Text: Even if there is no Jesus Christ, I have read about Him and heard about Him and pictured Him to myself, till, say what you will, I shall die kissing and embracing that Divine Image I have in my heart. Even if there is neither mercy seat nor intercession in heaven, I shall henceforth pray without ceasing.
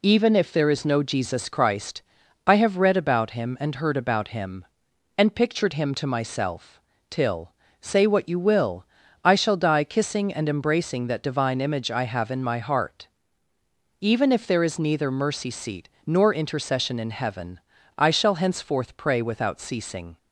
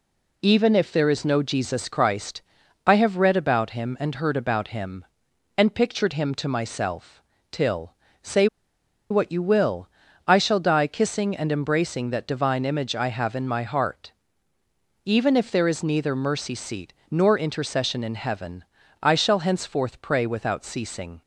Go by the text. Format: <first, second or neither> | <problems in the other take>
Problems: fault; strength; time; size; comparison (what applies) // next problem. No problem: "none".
first | pauses between "say" and "what"; noticeable; at 8.4 s; 0.64 s long // pauses between "seat" and "nor"; slight; at 16.9 s; 0.20 s long; slight in the first